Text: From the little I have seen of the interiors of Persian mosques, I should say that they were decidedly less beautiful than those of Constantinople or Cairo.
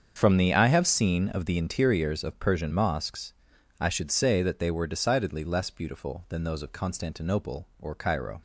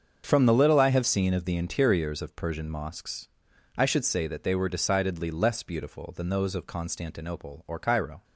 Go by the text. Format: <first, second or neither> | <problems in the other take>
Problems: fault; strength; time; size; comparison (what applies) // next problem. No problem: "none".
second | starts louder than the rest; strong; until 1.2 s; 7 dB; also in the second // skips "little"; at 0.5 s